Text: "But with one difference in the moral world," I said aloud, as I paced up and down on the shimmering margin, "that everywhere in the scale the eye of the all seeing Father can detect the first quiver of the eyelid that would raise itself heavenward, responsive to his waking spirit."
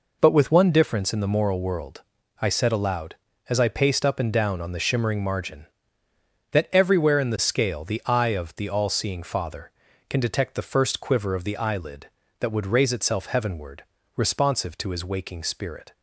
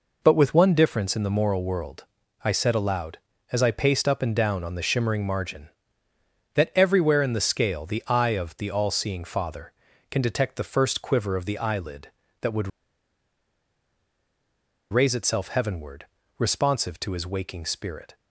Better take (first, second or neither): first